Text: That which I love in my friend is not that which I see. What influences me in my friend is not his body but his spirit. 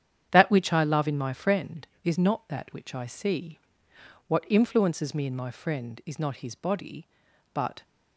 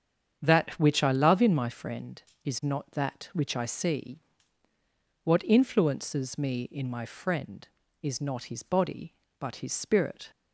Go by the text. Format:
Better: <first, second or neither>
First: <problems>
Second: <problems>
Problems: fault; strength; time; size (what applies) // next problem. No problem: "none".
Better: second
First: starts louder than the rest; strong; until 1.3 s; 9 dB // stops before "his spirit"; at 7.8 s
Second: starts louder than the rest; strong; until 1.4 s; 8 dB